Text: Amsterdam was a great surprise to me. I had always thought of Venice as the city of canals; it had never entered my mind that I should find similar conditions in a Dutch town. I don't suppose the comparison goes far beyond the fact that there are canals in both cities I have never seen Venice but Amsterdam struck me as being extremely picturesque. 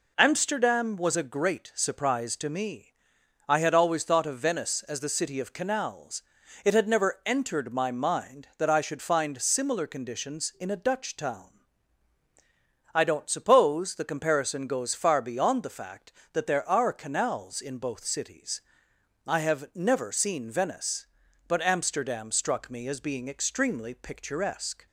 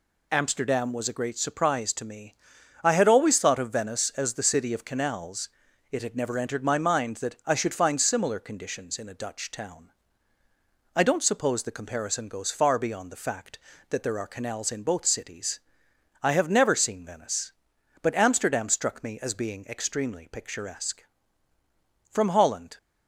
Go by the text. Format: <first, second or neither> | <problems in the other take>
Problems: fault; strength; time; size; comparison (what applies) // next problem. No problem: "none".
first | pauses between "cities" and "I"; noticeable; at 15.5 s; 0.64 s long; noticeable in the first // goes on to say "From Holland"; noticeable; from 22.0 s on; 0.68 s long